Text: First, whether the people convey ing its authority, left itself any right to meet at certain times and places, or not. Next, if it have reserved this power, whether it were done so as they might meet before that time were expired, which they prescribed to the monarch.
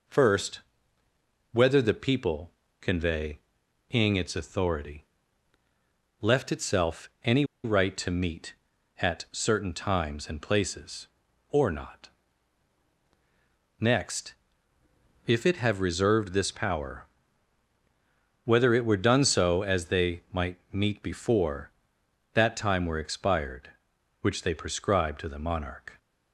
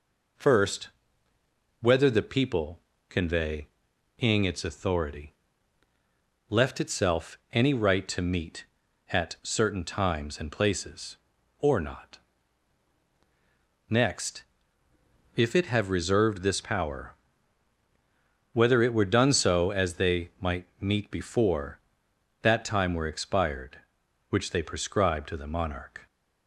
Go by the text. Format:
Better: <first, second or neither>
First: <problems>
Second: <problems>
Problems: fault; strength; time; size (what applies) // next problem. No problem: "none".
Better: second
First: pauses between "people" and "convey"; slight; at 2.5 s; 0.28 s long // pauses between "convey" and "ing"; noticeable; at 3.3 s; 0.50 s long // pauses between "any" and "right"; slight; at 7.4 s; 0.19 s long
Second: pauses between "people" and "convey"; slight; at 2.8 s; 0.28 s long // pauses between "convey" and "ing"; noticeable; at 3.6 s; 0.50 s long